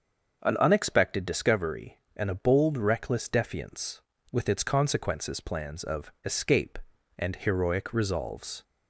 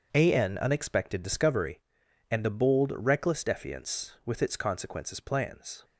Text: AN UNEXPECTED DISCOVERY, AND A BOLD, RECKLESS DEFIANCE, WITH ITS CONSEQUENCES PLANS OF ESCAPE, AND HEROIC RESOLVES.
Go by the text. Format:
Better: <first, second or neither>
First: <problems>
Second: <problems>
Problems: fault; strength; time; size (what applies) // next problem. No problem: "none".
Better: first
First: starts louder than the rest; until 1.4 s; 6.5 dB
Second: starts louder than the rest; until 1.1 s; 6.5 dB // stops before "OF ESCAPE AND HEROIC RESOLVES"; at 5.8 s